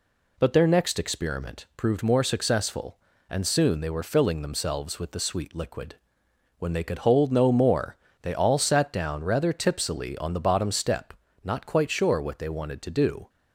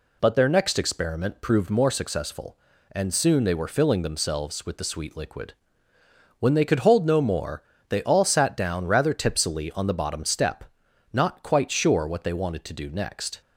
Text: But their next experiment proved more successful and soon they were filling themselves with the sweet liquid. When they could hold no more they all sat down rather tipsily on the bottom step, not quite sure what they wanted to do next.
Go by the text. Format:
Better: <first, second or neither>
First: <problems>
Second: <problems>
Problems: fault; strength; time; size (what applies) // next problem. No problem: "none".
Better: second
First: pauses between "more" and "they"; slight; at 7.9 s; 0.24 s long // stops before "next"; at 13.2 s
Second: pauses between "more" and "they"; slight; at 7.6 s; 0.26 s long